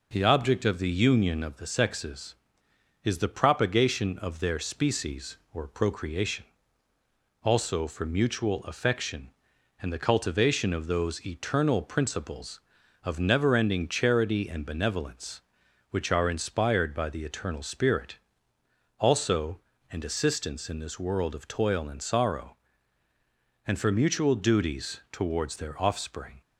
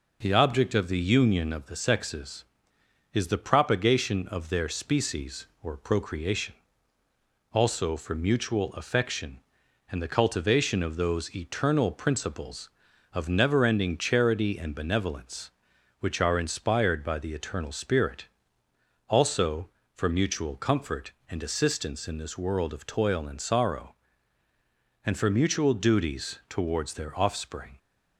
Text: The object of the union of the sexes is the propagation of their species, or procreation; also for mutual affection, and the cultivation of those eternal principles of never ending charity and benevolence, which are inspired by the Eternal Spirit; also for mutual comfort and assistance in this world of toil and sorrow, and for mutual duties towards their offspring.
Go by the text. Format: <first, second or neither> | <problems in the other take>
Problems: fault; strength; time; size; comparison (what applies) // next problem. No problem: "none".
second | skips "for mutual comfort"; at 19.7 s